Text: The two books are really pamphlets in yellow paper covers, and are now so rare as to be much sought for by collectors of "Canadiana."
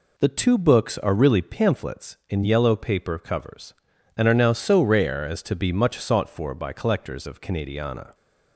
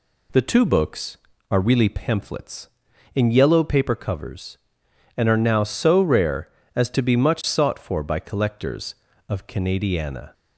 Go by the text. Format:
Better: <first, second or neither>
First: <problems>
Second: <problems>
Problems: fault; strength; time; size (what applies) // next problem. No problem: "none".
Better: neither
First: none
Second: none